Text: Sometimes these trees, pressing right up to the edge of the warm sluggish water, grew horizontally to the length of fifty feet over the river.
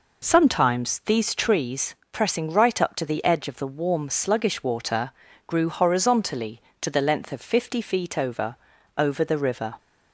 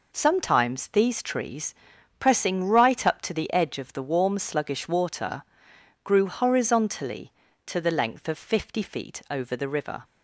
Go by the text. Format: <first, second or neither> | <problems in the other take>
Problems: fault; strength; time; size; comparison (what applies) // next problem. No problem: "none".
second | says "over" twice; at 8.9 s